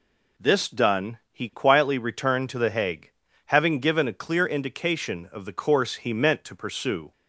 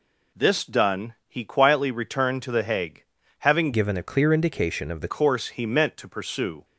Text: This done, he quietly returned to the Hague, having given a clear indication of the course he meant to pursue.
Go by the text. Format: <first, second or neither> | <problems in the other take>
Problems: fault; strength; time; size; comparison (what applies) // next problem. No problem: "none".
first | changes voice from "given" to "the"; from 3.7 to 5.0 s; 1.3 s long